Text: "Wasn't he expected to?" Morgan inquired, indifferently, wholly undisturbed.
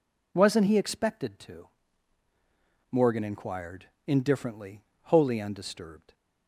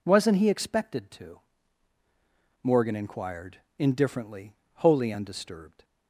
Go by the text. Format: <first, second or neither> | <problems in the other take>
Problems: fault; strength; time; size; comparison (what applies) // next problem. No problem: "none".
neither | none